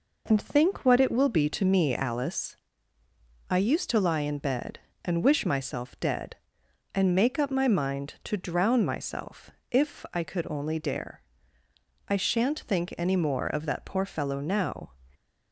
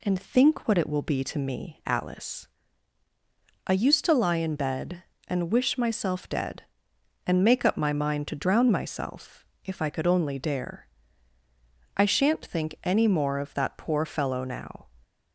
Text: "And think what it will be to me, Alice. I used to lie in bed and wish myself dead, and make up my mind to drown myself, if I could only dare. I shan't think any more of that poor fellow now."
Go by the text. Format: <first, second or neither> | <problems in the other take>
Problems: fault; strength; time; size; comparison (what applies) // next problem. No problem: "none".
neither | none